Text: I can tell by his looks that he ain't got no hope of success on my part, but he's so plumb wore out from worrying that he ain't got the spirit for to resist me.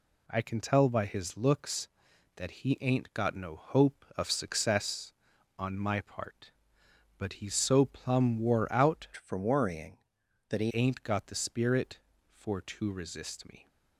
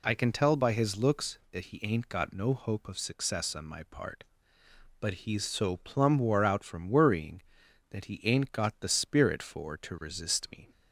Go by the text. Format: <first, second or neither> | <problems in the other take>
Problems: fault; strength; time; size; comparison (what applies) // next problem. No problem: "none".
second | changes voice from "from" to "he"; from 9.1 to 10.7 s; 1.6 s long